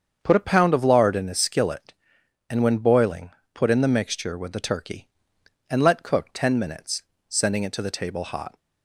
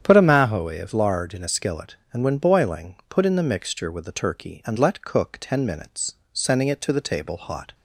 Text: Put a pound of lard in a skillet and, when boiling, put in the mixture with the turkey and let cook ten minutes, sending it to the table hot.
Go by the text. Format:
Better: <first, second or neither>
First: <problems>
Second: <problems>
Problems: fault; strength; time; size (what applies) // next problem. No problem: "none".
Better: first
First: starts louder than the rest; until 1.2 s; 7 dB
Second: starts louder than the rest; strong; until 1.0 s; 8.5 dB // says "mahoe" for "pound"; at 0.2 s